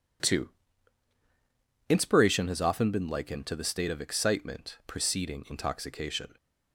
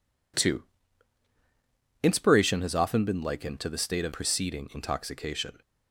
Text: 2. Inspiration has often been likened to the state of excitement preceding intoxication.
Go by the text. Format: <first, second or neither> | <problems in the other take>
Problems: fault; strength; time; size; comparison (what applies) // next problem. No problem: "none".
first | skips "excitement"; at 4.1 s